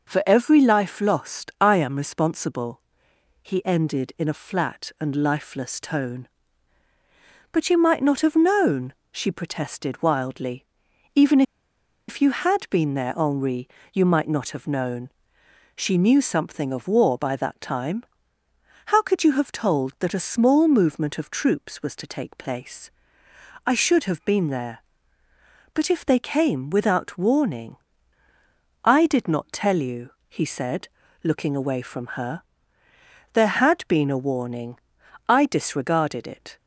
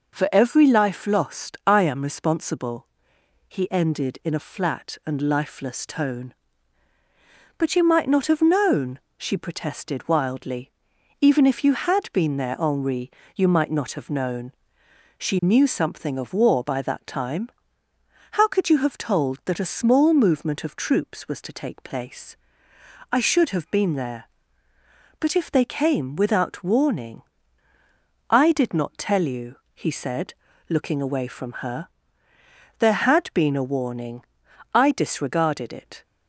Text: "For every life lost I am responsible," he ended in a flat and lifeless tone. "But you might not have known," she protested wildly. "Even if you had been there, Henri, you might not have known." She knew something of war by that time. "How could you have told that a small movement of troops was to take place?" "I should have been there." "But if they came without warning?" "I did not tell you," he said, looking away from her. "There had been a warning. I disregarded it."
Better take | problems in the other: second | pauses between "Even" and "if"; noticeable; at 11.4 s; 0.66 s long

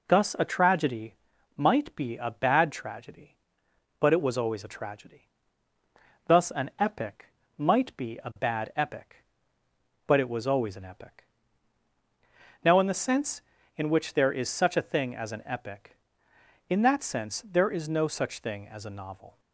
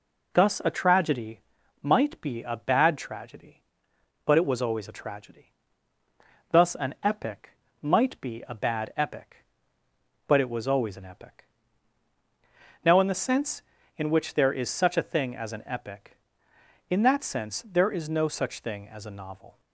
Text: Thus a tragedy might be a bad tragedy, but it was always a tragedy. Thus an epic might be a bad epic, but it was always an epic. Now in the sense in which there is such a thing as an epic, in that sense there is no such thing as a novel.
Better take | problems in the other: neither | pauses between "tragedy" and "might"; the same in both // pauses between "epic" and "might"; slight; the same in both

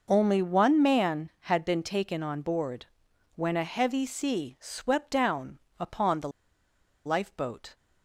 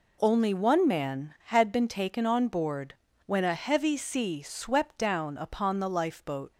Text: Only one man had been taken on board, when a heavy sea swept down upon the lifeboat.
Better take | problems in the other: second | pauses between "down" and "upon"; slight; at 5.5 s; 0.20 s long // pauses between "the" and "lifeboat"; noticeable; at 6.2 s; 0.76 s long

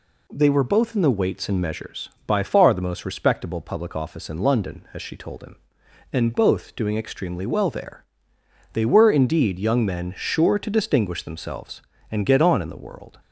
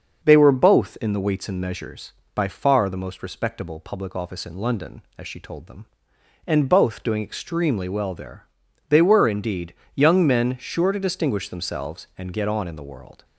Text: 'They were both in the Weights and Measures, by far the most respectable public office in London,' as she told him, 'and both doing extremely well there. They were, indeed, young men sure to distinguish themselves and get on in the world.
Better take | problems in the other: first | starts louder than the rest; until 1.3 s; 6.5 dB // says "them" for "him"; at 5.6 s

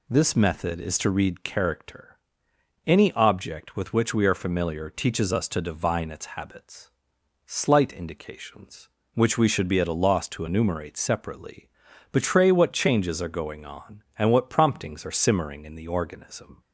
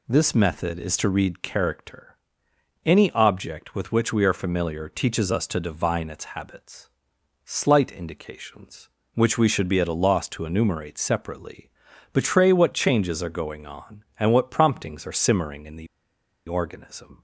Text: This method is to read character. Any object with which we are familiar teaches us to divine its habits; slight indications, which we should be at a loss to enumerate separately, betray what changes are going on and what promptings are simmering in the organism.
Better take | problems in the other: first | pauses between "the" and "organism"; noticeable; at 15.8 s; 0.62 s long

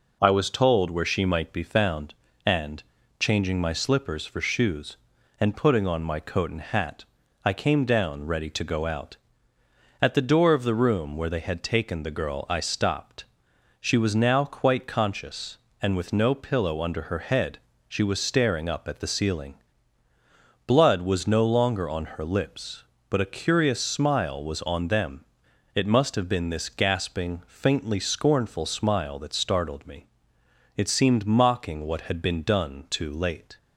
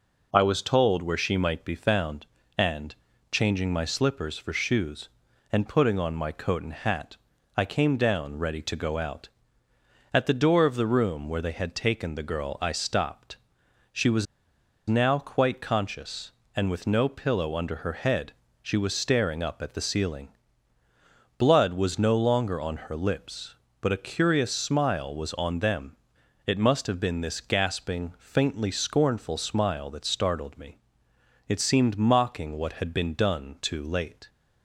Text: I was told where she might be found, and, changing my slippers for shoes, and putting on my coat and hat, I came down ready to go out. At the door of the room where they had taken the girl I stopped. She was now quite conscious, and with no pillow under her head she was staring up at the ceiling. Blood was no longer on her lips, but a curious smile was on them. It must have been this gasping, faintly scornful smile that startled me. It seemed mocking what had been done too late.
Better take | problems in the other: first | pauses between "was" and "now"; noticeable; at 14.2 s; 0.63 s long // pauses between "head" and "she"; slight; at 18.3 s; 0.28 s long; slight in the first

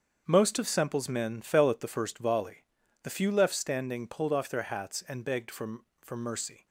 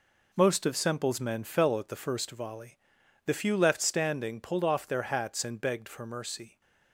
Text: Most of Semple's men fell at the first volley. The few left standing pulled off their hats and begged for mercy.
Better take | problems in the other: second | starts louder than the rest; until 1.2 s; 7 dB // says "for" twice; at 6.0 s

